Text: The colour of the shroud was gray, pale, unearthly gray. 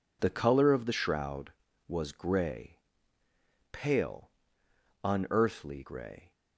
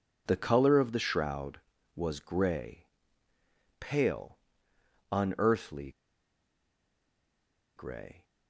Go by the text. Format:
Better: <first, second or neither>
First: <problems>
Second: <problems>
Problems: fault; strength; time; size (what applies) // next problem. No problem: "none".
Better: first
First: none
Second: pauses between "unearthly" and "gray"; strong; at 5.9 s; 1.8 s long